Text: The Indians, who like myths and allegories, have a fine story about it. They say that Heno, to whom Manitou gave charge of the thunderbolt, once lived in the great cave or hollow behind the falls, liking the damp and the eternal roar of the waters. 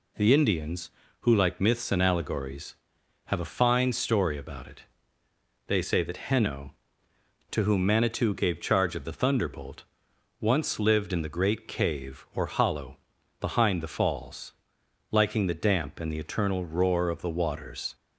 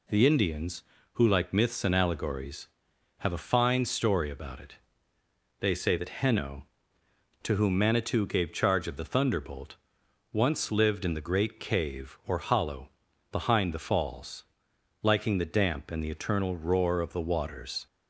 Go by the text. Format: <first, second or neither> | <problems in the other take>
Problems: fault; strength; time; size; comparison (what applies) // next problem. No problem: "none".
neither | pauses between "hollow" and "behind"; the same in both